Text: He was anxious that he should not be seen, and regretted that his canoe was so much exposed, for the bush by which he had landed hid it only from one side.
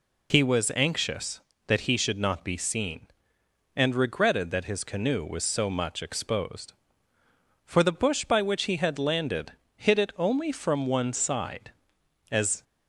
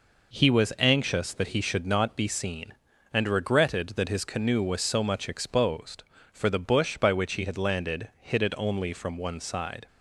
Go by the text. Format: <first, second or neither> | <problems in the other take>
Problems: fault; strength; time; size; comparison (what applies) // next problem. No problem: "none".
second | pauses between "landed" and "hid"; slight; at 9.5 s; 0.24 s long // goes on to say "As"; slight; from 12.3 s on; 0.32 s long